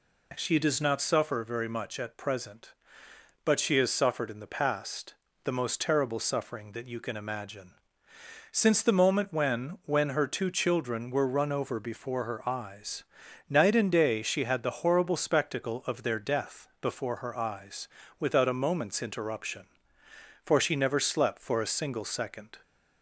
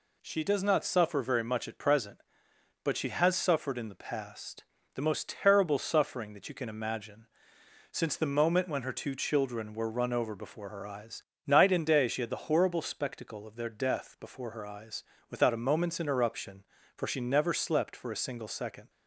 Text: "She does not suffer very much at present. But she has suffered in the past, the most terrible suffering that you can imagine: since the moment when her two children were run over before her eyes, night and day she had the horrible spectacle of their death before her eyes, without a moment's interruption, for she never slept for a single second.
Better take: second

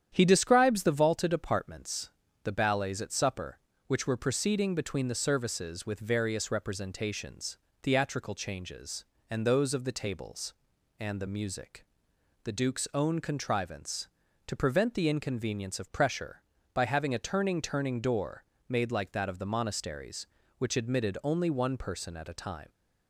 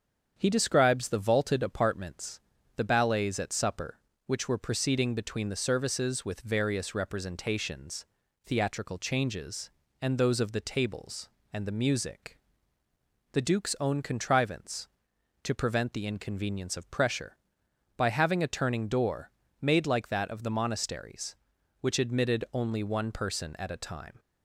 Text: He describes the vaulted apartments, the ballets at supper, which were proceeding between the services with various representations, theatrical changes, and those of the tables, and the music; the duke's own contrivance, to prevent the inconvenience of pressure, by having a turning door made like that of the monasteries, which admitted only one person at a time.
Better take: second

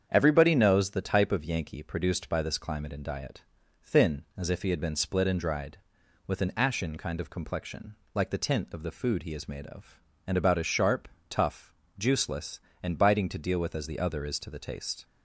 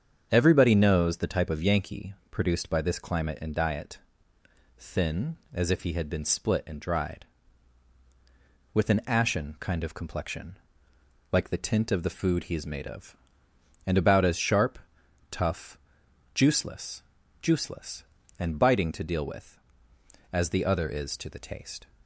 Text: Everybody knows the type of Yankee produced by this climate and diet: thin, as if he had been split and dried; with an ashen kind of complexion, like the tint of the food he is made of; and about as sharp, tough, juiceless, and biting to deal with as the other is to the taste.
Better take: first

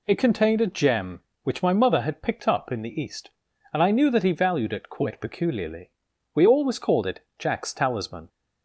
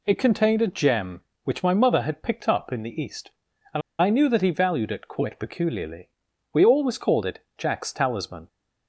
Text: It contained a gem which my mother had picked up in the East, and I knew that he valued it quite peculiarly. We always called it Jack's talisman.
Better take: first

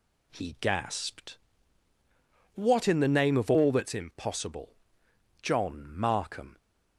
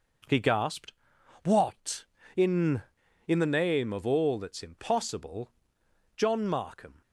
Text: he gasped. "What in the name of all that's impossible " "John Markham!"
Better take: first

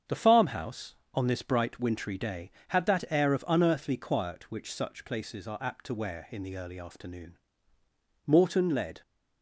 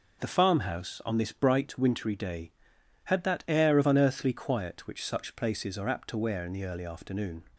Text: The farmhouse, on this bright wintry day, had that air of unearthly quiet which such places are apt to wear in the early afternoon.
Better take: second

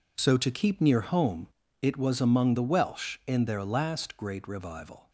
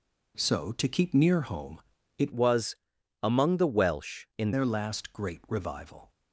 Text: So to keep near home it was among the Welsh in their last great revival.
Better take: first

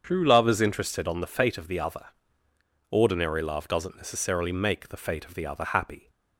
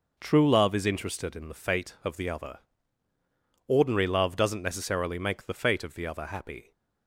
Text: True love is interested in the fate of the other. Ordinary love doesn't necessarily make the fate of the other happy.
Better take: second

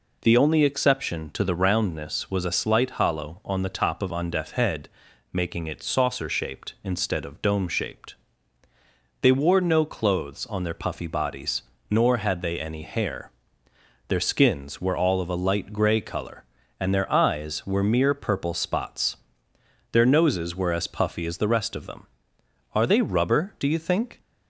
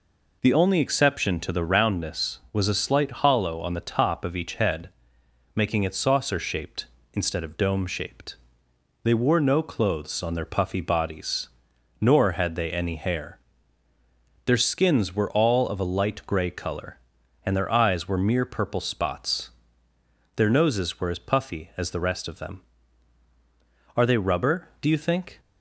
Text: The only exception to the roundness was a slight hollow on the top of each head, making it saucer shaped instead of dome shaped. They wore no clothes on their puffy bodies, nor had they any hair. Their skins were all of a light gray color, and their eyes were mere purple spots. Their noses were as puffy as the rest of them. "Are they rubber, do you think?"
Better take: second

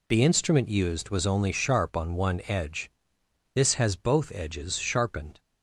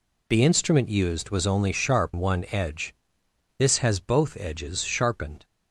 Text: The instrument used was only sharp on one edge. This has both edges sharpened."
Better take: first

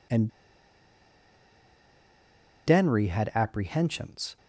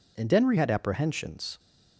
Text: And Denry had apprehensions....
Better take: second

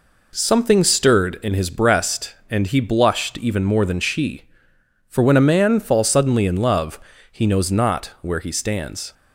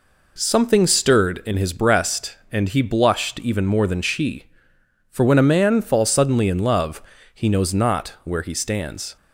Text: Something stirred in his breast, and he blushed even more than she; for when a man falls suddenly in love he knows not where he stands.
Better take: neither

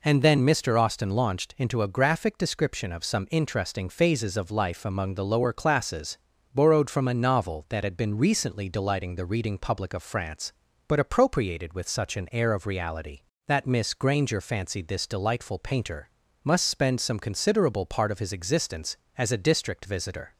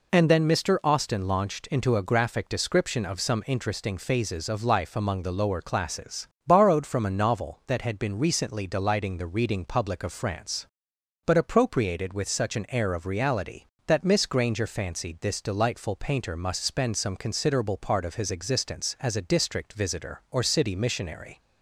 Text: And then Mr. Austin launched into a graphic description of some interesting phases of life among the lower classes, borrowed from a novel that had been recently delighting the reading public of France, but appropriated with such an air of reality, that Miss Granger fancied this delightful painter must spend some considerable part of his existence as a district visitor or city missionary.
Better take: second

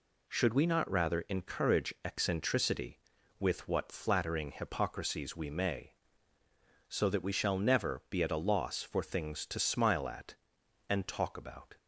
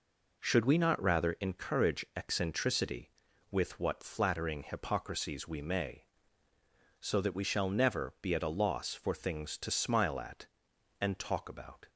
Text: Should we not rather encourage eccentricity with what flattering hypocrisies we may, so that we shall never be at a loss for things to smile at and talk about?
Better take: first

